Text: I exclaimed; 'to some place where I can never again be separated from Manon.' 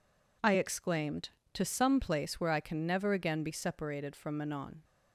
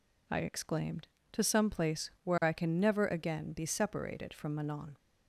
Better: neither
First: none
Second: none

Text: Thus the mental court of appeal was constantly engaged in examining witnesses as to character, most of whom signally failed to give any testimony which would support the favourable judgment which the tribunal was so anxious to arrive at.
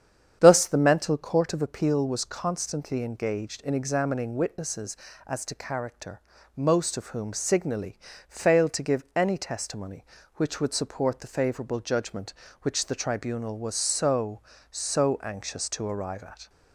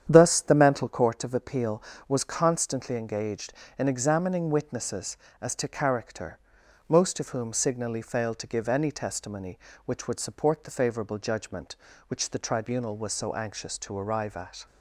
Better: second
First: starts louder than the rest; strong; until 1.4 s; 8.5 dB // pauses between "signally" and "failed"; slight; at 7.9 s; 0.32 s long // says "so" twice; at 14.7 s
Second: starts louder than the rest; strong; until 1.1 s; 9 dB

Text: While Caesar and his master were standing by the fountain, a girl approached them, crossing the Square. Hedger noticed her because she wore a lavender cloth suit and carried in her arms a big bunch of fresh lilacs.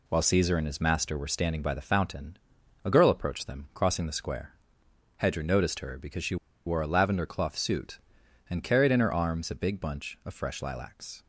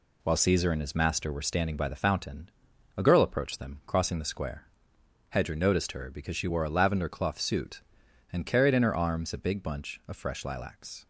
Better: second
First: pauses between "she" and "wore"; slight; at 6.3 s; 0.30 s long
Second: none

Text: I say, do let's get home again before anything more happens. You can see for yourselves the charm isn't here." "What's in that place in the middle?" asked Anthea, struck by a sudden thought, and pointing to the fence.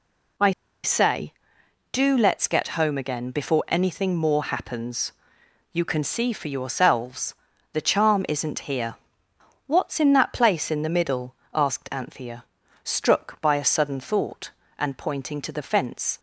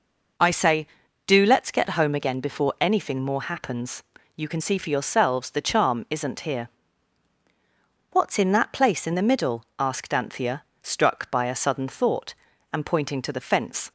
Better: second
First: pauses between "I" and "say"; slight; at 0.5 s; 0.33 s long // pauses between "yourselves" and "the"; slight; at 7.3 s; 0.36 s long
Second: none

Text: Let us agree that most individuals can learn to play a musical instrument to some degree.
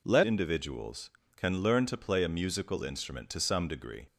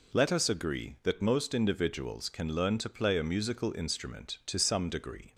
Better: second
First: skips "us agree that most"; at 0.2 s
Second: none

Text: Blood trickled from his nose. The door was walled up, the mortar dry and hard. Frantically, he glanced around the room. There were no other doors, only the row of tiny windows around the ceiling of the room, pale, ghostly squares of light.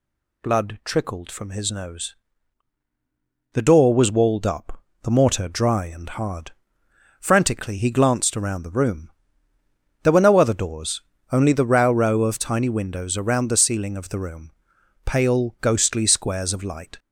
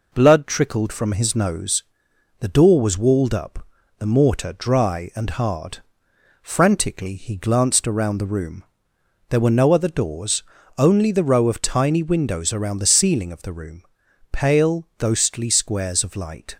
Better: second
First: says "row" twice; at 11.9 s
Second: none

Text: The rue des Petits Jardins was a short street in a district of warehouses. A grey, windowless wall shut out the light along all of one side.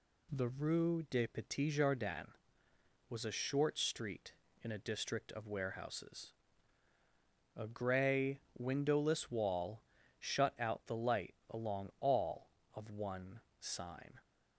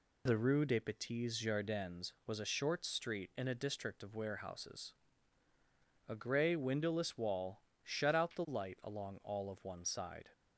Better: second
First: pauses between "wall" and "shut"; at 9.8 s; 0.38 s long // pauses between "light" and "along"; slight; at 11.3 s; 0.16 s long // says "sign" for "side"; at 13.5 s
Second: pauses between "wall" and "shut"; slight; at 7.6 s; 0.24 s long

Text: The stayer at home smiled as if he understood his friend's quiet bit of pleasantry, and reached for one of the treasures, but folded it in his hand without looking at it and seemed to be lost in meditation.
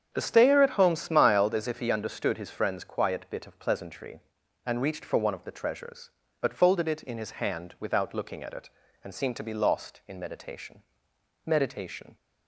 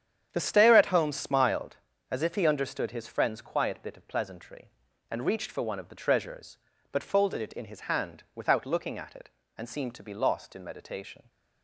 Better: second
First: starts louder than the rest; strong; until 1.1 s; 8 dB // says "meditation" twice; at 11.4 s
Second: starts louder than the rest; strong; until 1.3 s; 8.5 dB

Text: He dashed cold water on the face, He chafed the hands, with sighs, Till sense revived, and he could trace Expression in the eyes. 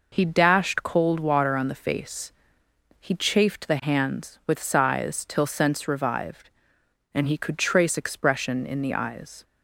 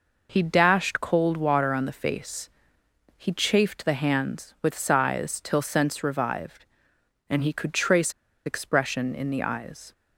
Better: first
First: none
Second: pauses between "trace" and "Expression"; slight; at 8.1 s; 0.33 s long

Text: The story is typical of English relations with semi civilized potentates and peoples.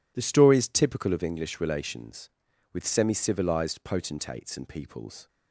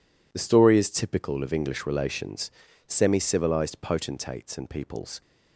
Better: first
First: none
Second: skips "with"; at 2.6 s

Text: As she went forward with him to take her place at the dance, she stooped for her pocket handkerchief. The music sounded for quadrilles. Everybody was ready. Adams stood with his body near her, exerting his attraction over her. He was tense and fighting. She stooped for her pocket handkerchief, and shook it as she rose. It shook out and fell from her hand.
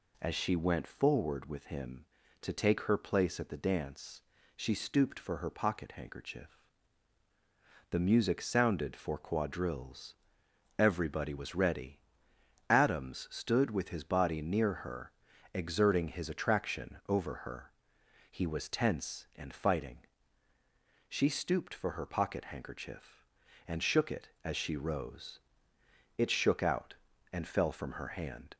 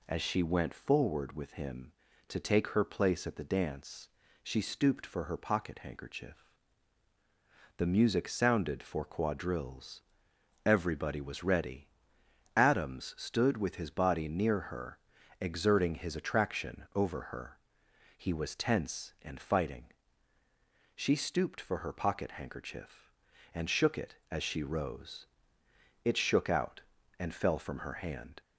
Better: neither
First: none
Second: none

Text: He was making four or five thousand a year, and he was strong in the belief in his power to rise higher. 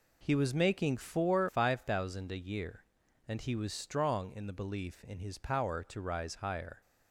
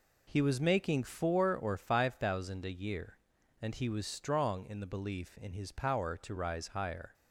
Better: second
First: skips "or"; at 1.4 s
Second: none

